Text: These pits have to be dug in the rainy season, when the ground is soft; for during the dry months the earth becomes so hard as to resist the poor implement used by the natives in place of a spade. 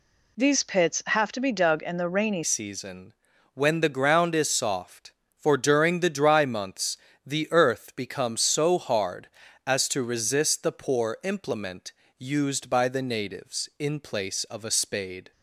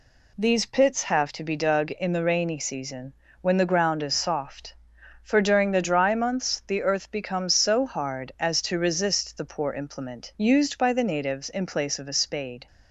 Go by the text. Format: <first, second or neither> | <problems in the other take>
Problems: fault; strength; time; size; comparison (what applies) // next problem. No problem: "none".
second | changes voice at "season"; from 2.4 s on; 12.9 s long // pauses between "months" and "the"; slight; at 6.9 s; 0.28 s long // pauses between "implement" and "used"; slight; at 11.9 s; 0.26 s long